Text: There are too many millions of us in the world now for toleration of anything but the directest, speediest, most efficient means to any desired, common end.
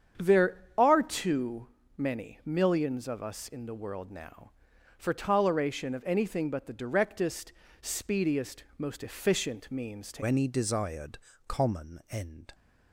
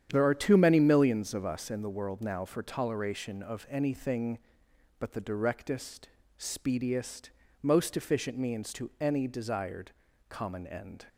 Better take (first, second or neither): second